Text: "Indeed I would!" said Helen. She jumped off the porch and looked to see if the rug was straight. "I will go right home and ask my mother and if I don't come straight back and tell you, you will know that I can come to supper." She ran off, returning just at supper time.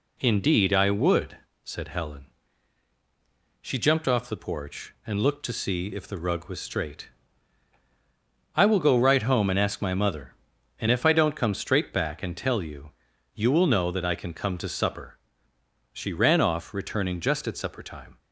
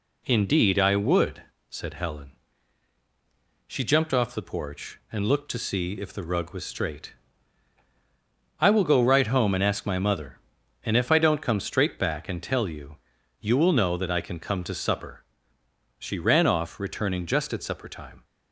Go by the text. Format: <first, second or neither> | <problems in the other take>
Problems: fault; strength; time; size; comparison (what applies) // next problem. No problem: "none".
neither | none